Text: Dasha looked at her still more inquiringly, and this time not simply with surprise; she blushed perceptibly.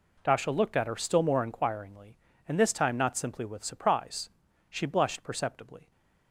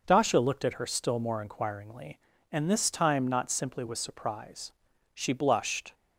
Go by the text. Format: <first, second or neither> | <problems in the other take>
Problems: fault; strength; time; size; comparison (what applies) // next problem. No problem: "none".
first | stops before "perceptibly"; at 5.9 s